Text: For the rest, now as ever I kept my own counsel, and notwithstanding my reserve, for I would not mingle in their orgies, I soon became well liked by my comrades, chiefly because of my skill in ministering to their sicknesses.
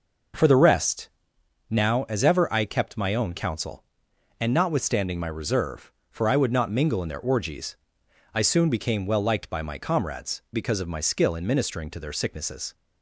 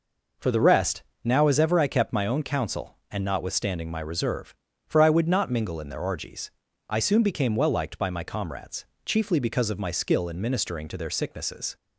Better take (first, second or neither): second